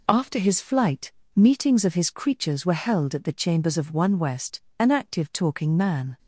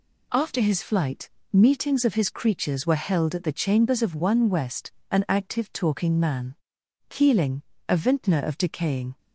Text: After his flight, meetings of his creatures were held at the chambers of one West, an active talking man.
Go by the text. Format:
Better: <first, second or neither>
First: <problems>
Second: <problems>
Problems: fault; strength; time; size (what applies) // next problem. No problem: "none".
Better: first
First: none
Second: goes on to say "Keeling a vintner of decaying"; strong; from 7.0 s on; 2.1 s long